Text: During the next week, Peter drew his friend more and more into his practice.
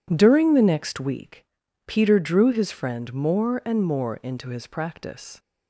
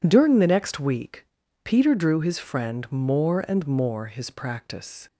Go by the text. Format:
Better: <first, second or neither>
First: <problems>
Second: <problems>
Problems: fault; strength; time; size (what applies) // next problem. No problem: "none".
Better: first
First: none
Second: skips "into"; at 4.0 s